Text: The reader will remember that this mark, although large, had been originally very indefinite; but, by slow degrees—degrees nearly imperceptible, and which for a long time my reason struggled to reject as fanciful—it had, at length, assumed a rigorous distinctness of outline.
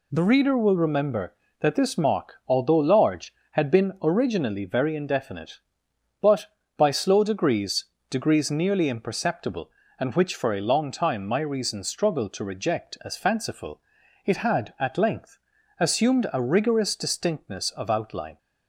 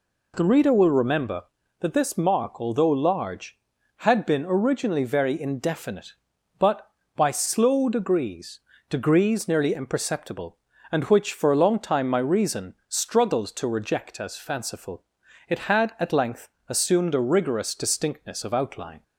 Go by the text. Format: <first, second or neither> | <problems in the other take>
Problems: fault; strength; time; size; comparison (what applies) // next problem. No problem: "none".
neither | none